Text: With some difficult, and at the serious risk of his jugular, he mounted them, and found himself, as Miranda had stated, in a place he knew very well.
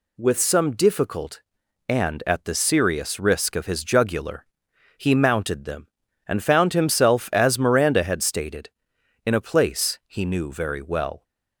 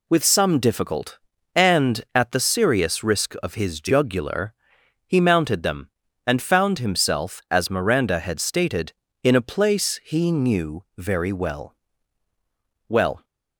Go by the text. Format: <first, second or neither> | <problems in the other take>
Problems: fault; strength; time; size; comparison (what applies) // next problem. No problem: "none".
first | says "well" twice; at 12.8 s